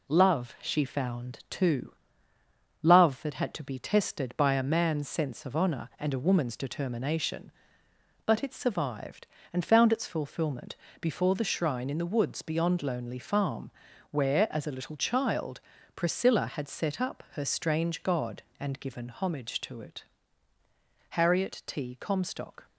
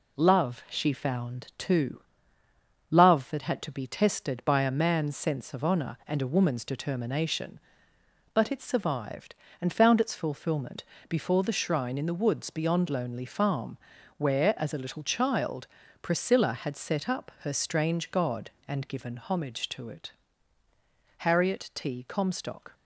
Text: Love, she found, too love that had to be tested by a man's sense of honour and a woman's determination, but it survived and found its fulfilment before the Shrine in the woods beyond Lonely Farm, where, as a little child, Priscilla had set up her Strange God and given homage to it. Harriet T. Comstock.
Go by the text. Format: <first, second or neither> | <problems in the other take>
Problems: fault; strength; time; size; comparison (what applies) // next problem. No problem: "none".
neither | pauses between "too" and "love"; noticeable; the same in both // pauses between "fulfilment" and "before"; slight; the same in both